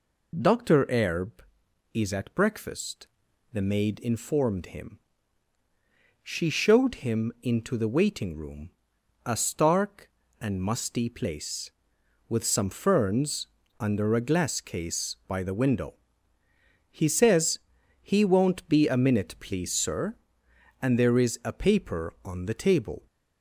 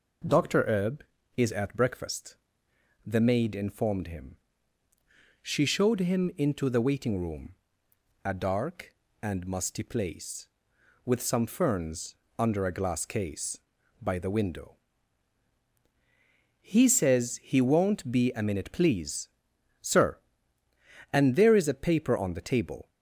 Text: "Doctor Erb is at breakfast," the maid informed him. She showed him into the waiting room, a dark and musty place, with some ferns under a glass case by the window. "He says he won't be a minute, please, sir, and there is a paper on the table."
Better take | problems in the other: second | says "stark" for "dark"; at 9.3 s // pauses between "ferns" and "under"; slight; at 13.4 s; 0.32 s long; slight in the second // pauses between "says" and "he"; at 17.6 s; 0.42 s long

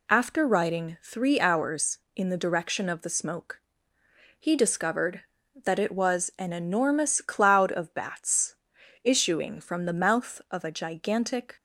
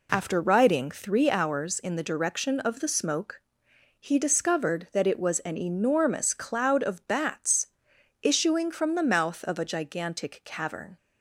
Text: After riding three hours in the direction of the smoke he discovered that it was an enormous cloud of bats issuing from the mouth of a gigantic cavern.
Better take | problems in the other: second | pauses between "smoke" and "he"; noticeable; at 3.5 s; 0.78 s long; noticeable in the second // pauses between "bats" and "issuing"; noticeable; at 8.5 s; 0.48 s long; noticeable in the second // stops before "cavern"; at 11.5 s

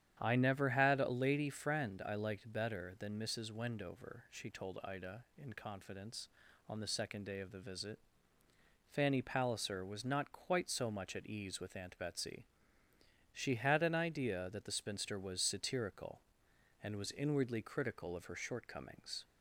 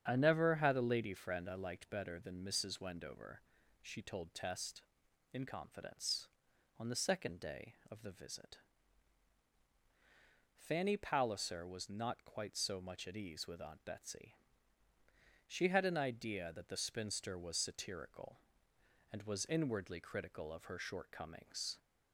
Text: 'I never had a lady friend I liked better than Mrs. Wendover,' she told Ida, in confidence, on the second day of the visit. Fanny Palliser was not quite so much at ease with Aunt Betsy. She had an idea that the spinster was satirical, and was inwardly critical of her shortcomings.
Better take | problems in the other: first | starts louder than the rest; strong; until 1.1 s; 8 dB; strong in the first // says "Test" for "Ida"; at 4.3 s

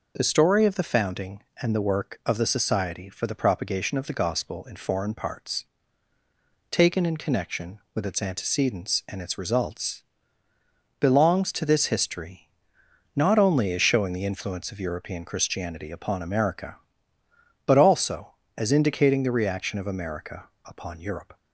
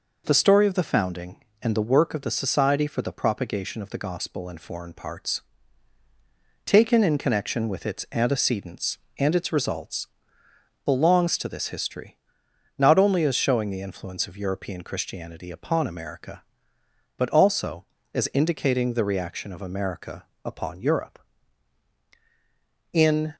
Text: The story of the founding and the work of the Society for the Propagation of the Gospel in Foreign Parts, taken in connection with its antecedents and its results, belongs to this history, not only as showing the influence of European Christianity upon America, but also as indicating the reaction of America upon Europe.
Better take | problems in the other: first | pauses between "America" and "upon"; slight; at 20.2 s; 0.18 s long; slight in the first // goes on to say "In"; slight; from 22.9 s on; 0.42 s long

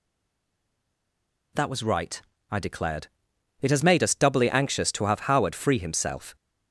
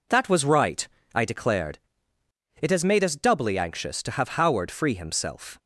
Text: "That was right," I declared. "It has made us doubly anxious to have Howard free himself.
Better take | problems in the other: second | stays silent before the first word; noticeable; until 1.5 s; 1.5 s long

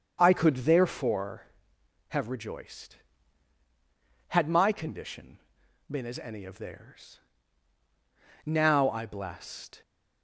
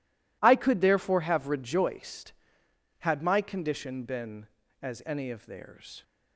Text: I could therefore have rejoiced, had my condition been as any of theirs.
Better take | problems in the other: second | starts louder than the rest; until 1.2 s; 7 dB // pauses between "condition" and "been"; noticeable; at 5.3 s; 0.52 s long // goes on to say "Now I blessed"; from 8.4 s on; 1.3 s long

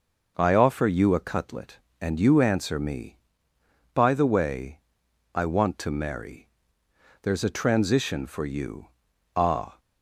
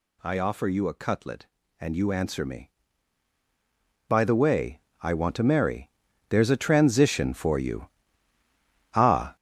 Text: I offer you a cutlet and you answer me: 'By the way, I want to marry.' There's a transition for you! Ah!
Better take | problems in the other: first | gets louder; strong; throughout; 8 dB

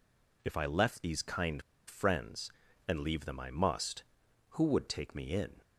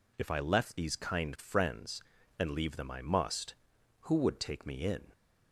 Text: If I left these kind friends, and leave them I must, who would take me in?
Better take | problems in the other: second | pauses between "kind" and "friends"; slight; at 1.6 s; 0.25 s long

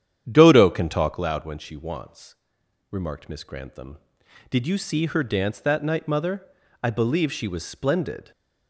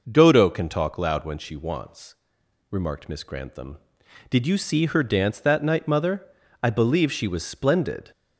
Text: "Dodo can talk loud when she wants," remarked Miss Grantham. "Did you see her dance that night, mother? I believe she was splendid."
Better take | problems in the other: second | starts louder than the rest; strong; until 1.3 s; 9.5 dB

